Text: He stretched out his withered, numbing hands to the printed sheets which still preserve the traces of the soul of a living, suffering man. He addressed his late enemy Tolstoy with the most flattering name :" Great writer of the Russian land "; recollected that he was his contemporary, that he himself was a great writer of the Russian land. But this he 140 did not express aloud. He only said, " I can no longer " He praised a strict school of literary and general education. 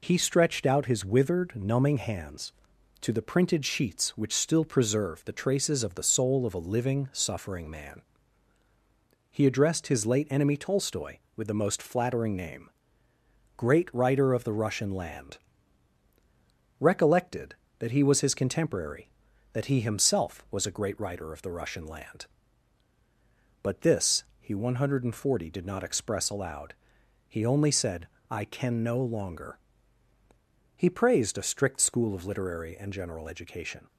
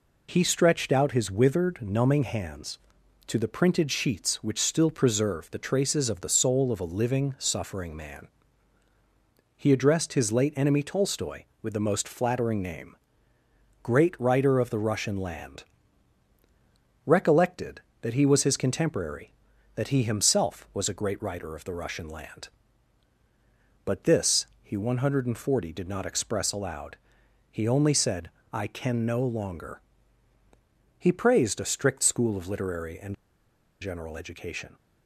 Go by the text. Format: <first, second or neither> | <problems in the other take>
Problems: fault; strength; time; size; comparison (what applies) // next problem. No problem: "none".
first | pauses between "this" and "he"; slight; at 24.4 s; 0.16 s long; slight in the first // pauses between "and" and "general"; noticeable; at 33.1 s; 0.66 s long